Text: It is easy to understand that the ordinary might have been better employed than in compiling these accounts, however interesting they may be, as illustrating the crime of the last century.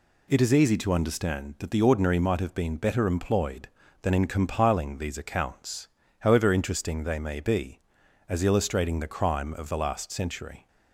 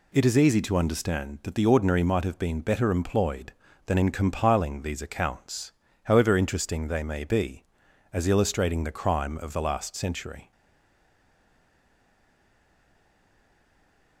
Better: first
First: none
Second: stays silent after the last word; strong; from 10.5 s on; 3.7 s long

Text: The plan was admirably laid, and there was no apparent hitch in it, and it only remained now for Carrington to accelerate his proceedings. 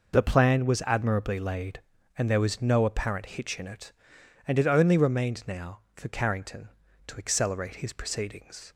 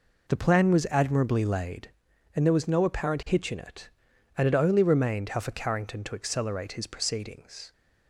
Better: first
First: none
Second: says "how" for "now"; at 5.3 s

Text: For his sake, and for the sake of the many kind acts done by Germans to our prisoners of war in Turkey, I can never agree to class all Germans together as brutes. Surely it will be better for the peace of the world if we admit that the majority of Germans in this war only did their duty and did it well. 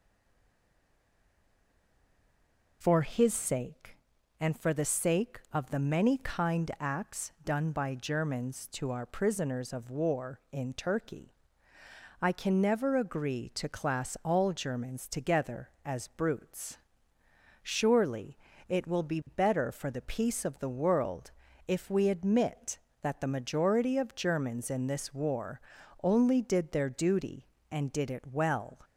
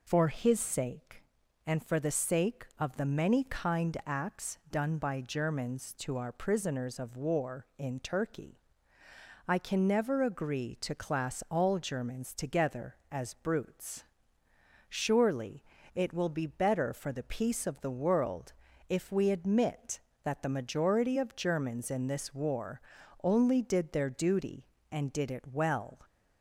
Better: second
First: stays silent before the first word; strong; until 2.8 s; 2.8 s long // pauses between "acts" and "done"; slight; at 7.2 s; 0.16 s long // pauses between "Surely" and "it"; slight; at 18.3 s; 0.32 s long // pauses between "world" and "if"; slight; at 21.3 s; 0.34 s long // pauses between "war" and "only"; at 25.6 s; 0.44 s long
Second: pauses between "acts" and "done"; slight; at 4.5 s; 0.16 s long // pauses between "Surely" and "it"; slight; at 15.6 s; 0.32 s long // pauses between "world" and "if"; slight; at 18.5 s; 0.34 s long // pauses between "war" and "only"; at 22.8 s; 0.44 s long

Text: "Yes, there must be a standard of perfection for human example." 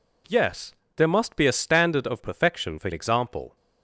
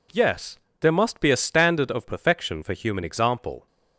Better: second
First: skips "human"; at 2.9 s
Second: none

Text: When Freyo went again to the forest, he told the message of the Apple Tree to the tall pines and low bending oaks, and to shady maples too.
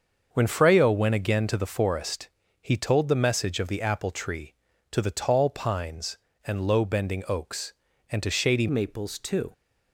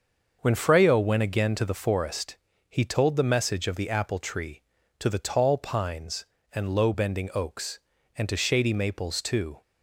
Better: second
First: starts louder than the rest; until 1.3 s; 6.5 dB // changes voice at "maples"; from 8.6 s on; 0.9 s long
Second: starts louder than the rest; until 1.4 s; 6.5 dB

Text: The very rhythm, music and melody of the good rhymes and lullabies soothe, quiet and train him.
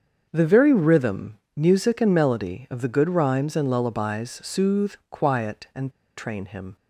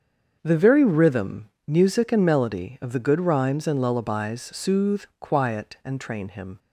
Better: second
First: starts louder than the rest; until 1.3 s; 7 dB // pauses between "and" and "train"; slight; at 5.9 s; 0.26 s long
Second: starts louder than the rest; until 1.4 s; 7 dB

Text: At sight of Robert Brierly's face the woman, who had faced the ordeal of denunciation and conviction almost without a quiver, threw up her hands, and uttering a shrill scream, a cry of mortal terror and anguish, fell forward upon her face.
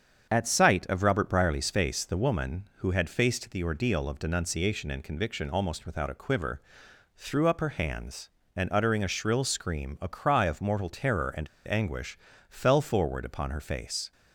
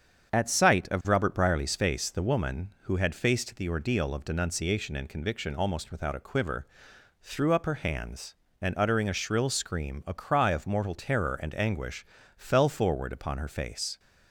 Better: second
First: starts louder than the rest; strong; until 1.3 s; 7.5 dB // pauses between "and" and "anguish"; slight; at 11.4 s; 0.18 s long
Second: starts louder than the rest; strong; until 1.3 s; 7.5 dB

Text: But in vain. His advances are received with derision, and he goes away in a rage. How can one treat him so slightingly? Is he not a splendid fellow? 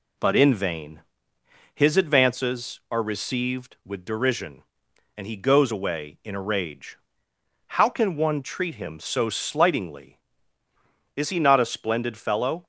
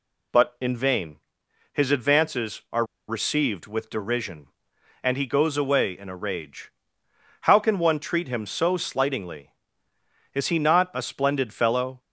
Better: first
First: none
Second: pauses between "are" and "received"; slight; at 2.8 s; 0.24 s long

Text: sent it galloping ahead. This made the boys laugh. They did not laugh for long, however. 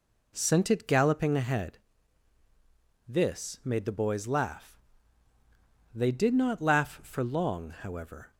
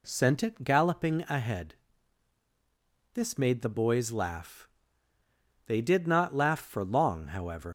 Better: first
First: none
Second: leaves "however" unfinished; at 7.6 s; 85 ms

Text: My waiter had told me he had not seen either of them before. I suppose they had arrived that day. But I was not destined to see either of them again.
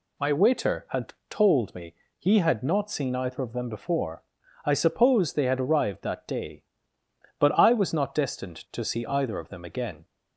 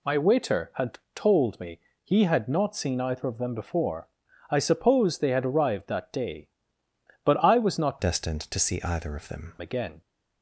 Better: first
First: pauses between "had" and "told"; slight; at 1.1 s; 0.16 s long // pauses between "me" and "he"; slight; at 1.9 s; 0.24 s long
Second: pauses between "had" and "told"; slight; at 0.9 s; 0.16 s long // pauses between "me" and "he"; slight; at 1.7 s; 0.24 s long // changes voice from "destined" to "them"; from 7.9 to 9.5 s; 1.6 s long

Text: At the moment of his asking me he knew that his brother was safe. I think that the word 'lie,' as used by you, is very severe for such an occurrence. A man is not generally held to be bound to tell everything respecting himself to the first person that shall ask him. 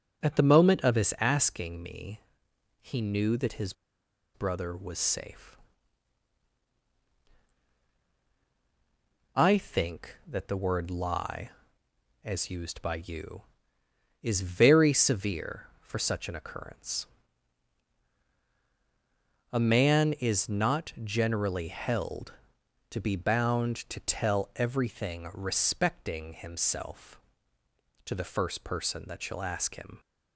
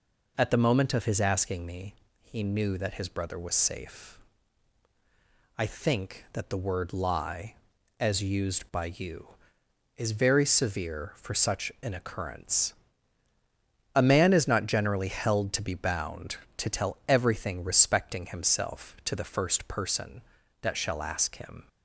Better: second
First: pauses between "me" and "he"; noticeable; at 2.2 s; 0.62 s long // pauses between "his" and "brother"; noticeable; at 3.7 s; 0.61 s long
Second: pauses between "me" and "he"; slight; at 1.9 s; 0.26 s long

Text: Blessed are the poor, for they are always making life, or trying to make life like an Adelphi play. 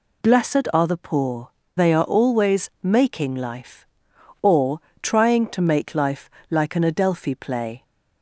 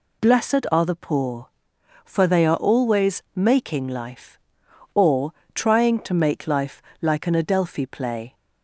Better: second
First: skips "for"; at 1.6 s // pauses between "or" and "trying"; slight; at 4.7 s; 0.24 s long // pauses between "life" and "like"; slight; at 6.2 s; 0.20 s long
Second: pauses between "or" and "trying"; slight; at 5.3 s; 0.24 s long // pauses between "life" and "like"; slight; at 6.8 s; 0.18 s long

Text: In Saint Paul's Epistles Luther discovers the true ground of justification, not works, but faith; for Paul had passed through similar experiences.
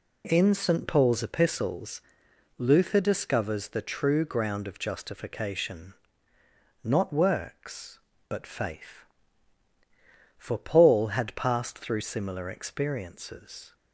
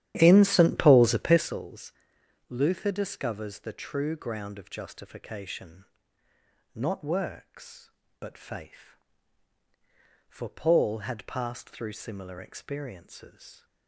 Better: first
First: pauses between "Epistles" and "Luther"; noticeable; at 2.0 s; 0.56 s long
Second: starts louder than the rest; strong; until 1.6 s; 11.5 dB // pauses between "Epistles" and "Luther"; noticeable; at 1.9 s; 0.56 s long

